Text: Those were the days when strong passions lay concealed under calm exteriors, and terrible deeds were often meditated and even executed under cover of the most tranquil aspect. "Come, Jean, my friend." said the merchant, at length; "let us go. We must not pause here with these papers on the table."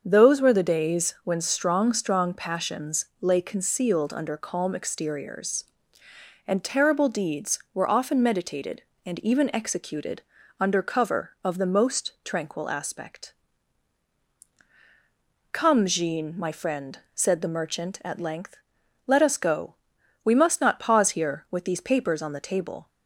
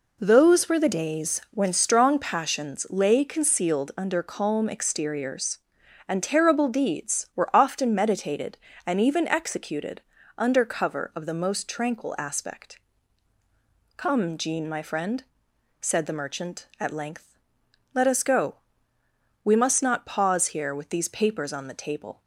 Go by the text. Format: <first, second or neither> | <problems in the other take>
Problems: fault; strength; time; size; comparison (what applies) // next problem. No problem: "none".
second | starts louder than the rest; until 1.0 s; 6.5 dB // says "strong" twice; at 1.9 s // pauses between "passions" and "lay"; slight; at 3.0 s; 0.16 s long // pauses between "executed" and "under"; at 10.2 s; 0.38 s long; slight in the second